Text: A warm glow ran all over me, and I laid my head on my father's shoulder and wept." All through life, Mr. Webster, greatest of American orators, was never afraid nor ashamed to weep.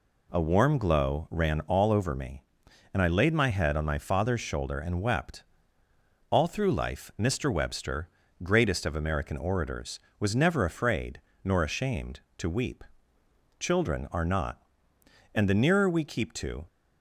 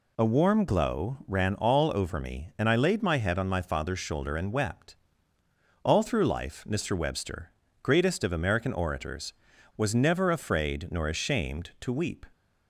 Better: second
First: pauses between "afraid" and "nor"; slight; at 11.2 s; 0.24 s long // goes on to say "Children are not and the nearer we keep to"; strong; from 13.5 s on; 3.0 s long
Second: none

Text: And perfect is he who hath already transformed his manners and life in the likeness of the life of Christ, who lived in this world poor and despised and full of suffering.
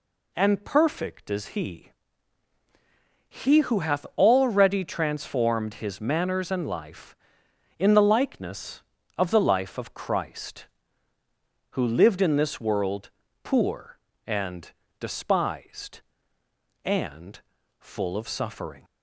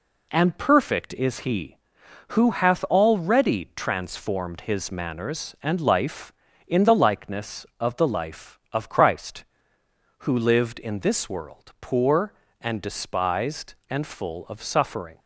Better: second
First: says "he" twice; at 3.3 s // pauses between "world" and "poor"; slight; at 13.0 s; 0.34 s long // pauses between "and" and "despised"; slight; at 14.7 s; 0.30 s long // pauses between "and" and "full"; at 17.4 s; 0.40 s long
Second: none

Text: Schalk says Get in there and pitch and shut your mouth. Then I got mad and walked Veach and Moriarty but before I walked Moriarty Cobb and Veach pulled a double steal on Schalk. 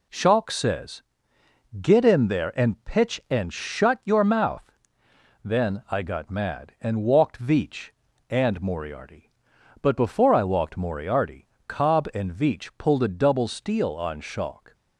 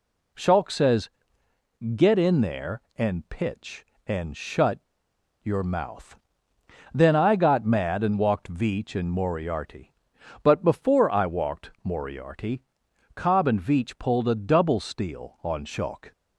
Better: first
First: pauses between "says" and "Get"; noticeable; at 1.0 s; 0.78 s long // pauses between "Moriarty" and "Cobb"; slight; at 11.4 s; 0.20 s long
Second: pauses between "says" and "Get"; noticeable; at 1.0 s; 0.86 s long // pauses between "shut" and "your"; noticeable; at 4.7 s; 0.65 s long // pauses between "Moriarty" and "Cobb"; noticeable; at 12.6 s; 0.54 s long

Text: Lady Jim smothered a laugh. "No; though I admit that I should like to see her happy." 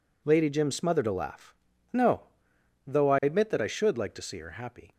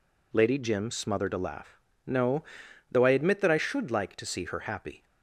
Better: neither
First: none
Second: none

